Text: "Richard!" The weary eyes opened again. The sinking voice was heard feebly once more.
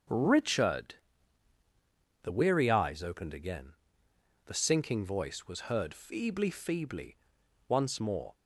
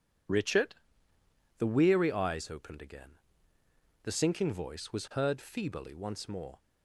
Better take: second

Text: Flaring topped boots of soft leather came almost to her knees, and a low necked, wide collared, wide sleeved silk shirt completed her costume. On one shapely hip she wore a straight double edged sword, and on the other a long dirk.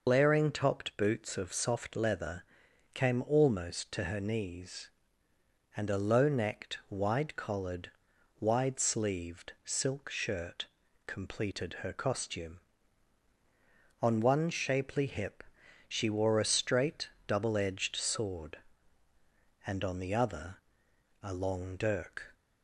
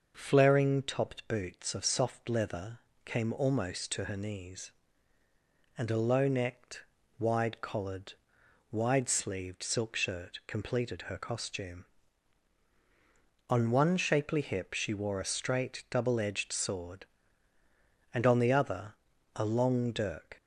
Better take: second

